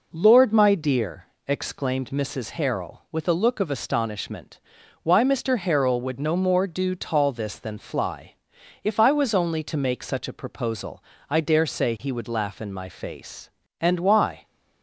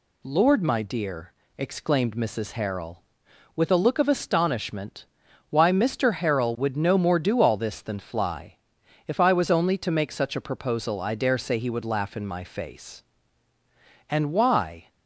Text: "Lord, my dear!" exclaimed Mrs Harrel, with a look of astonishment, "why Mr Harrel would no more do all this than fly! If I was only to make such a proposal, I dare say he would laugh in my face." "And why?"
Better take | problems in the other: second | says "tall" for "all"; at 6.9 s

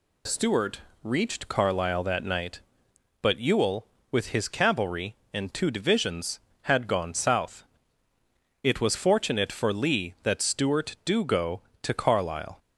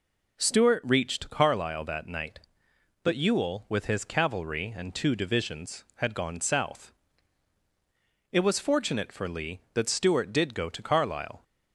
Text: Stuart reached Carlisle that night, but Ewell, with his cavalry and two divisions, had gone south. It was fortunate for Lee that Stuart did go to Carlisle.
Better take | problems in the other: second | pauses between "Stuart" and "reached"; slight; at 0.8 s; 0.24 s long // says "do" for "did"; at 11.0 s

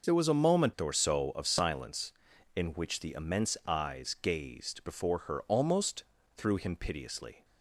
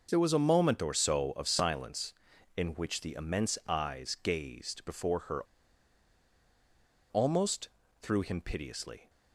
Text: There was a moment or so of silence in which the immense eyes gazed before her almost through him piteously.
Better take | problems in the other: first | pauses between "her" and "almost"; strong; at 5.4 s; 1.6 s long // pauses between "almost" and "through"; slight; at 7.6 s; 0.32 s long; slight in the first

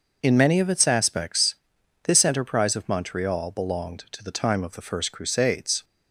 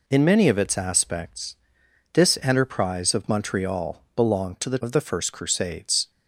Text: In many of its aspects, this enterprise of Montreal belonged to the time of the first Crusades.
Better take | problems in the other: first | skips "time"; at 4.7 s

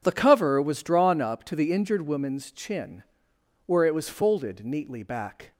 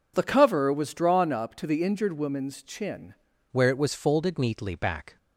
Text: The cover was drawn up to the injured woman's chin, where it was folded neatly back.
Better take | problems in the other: first | changes voice at "where"; from 3.5 s on; 1.6 s long

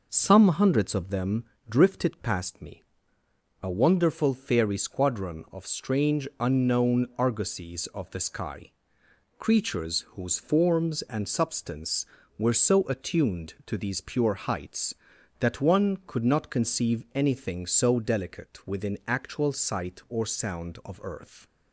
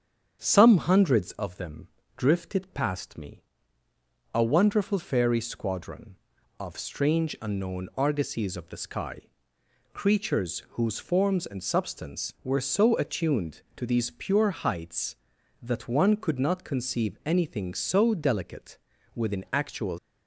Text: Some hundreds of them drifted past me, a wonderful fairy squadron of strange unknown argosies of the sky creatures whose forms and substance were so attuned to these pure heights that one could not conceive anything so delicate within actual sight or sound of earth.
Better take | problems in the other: first | starts louder than the rest; strong; until 1.4 s; 8 dB // pauses between "them" and "drifted"; slight; at 1.8 s; 0.28 s long; slight in the first // pauses between "sky" and "creatures"; noticeable; at 9.2 s; 0.72 s long; noticeable in the first // pauses between "creatures" and "whose"; slight; at 10.6 s; 0.16 s long // pauses between "delicate" and "within"; slight; at 18.7 s; 0.36 s long // stops before "sight or sound of earth"; at 19.9 s

